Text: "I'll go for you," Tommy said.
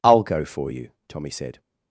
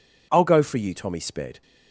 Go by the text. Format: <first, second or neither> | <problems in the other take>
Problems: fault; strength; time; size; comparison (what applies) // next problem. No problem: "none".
first | says "sped" for "said"; at 1.1 s